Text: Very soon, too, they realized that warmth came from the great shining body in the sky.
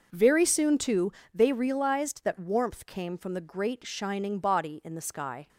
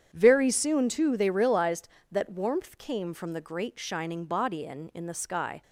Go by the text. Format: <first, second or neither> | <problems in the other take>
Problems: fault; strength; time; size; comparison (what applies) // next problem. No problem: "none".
first | starts louder than the rest; strong; until 1.1 s; 8.5 dB; noticeable in the first // says "in" twice; at 4.9 s